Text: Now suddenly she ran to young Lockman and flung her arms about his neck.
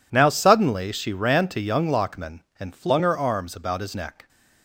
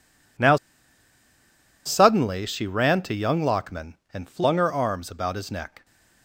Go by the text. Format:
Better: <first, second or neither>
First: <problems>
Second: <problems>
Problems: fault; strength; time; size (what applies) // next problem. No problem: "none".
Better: first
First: none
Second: pauses between "Now" and "suddenly"; strong; at 0.5 s; 1.3 s long